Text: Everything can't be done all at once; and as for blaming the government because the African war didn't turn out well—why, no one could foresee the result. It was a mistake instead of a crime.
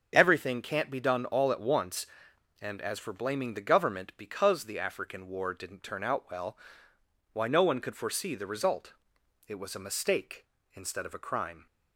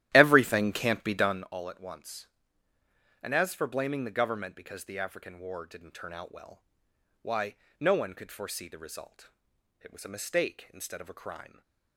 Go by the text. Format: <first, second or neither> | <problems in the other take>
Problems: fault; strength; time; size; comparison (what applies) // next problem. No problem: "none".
first | starts louder than the rest; strong; until 1.5 s; 12.5 dB